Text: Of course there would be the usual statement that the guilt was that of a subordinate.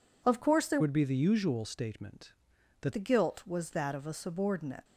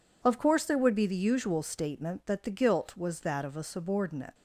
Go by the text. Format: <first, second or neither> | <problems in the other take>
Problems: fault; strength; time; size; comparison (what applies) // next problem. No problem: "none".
second | changes voice from "would" to "that"; from 0.7 to 2.9 s; 2.2 s long